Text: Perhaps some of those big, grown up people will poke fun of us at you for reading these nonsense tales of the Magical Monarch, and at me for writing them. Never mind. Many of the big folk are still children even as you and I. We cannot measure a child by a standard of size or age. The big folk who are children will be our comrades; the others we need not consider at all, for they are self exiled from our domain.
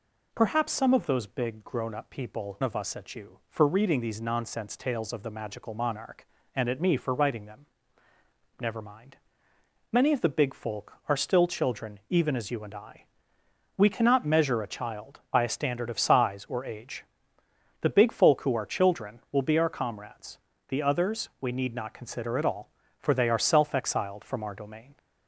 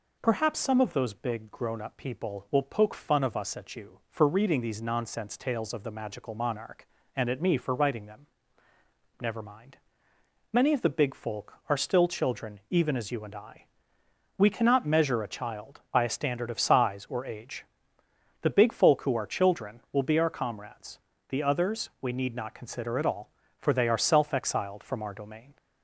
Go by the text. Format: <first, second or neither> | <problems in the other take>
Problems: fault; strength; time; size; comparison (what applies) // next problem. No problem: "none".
second | skips "will poke fun"; at 2.6 s